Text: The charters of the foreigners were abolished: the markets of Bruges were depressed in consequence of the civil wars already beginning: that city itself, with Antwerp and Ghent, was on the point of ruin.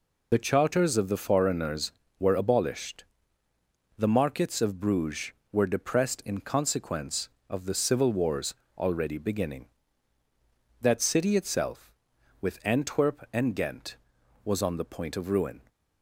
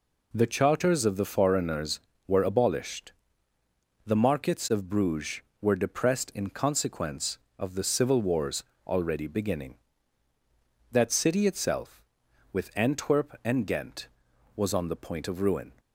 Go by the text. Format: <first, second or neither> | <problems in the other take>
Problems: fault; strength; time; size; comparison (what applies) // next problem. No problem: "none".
second | loses the start of "The"; at 0.3 s; 70 ms // pauses between "wars" and "already"; slight; at 8.5 s; 0.22 s long; slight in the second